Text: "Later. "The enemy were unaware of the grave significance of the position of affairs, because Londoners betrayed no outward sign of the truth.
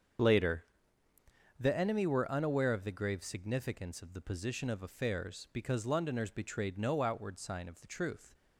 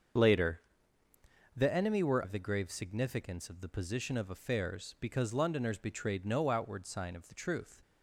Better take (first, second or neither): first